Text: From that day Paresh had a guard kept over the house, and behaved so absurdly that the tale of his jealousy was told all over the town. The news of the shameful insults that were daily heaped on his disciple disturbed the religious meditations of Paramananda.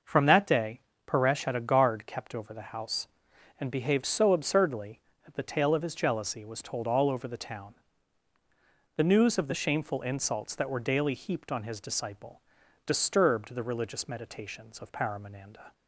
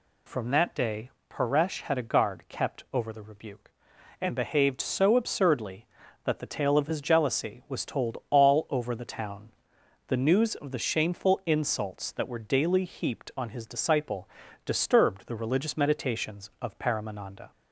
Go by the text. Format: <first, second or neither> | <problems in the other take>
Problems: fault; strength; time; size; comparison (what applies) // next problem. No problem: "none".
first | pauses between "day" and "Paresh"; slight; at 1.0 s; 0.22 s long; slight in the first // says "rebuke" for "house"; at 3.2 s // pauses between "disciple" and "disturbed"; at 14.2 s; 0.38 s long; also in the first